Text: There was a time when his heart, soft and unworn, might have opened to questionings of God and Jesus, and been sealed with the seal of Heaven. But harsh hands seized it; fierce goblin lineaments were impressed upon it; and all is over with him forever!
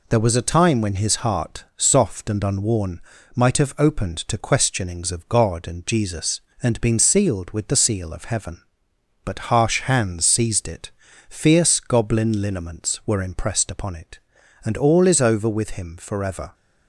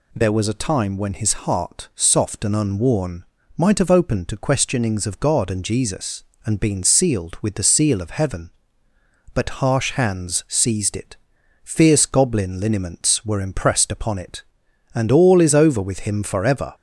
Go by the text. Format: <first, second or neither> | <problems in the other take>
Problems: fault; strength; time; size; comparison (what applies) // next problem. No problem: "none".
neither | none